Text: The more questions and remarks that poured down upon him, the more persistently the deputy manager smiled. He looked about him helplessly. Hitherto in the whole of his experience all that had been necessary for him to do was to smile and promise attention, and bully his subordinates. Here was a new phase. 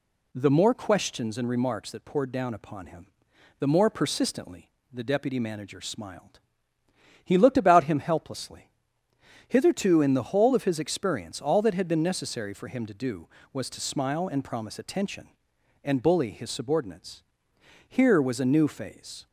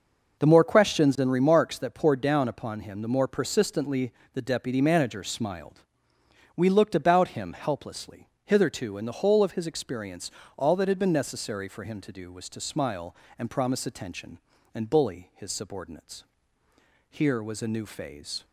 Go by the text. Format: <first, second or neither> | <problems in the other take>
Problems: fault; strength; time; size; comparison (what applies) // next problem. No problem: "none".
first | pauses between "persistently" and "the"; slight; at 4.1 s; 0.22 s long; slight in the first // says "We" for "He"; at 6.5 s // pauses between "experience" and "all"; slight; at 10.3 s; 0.26 s long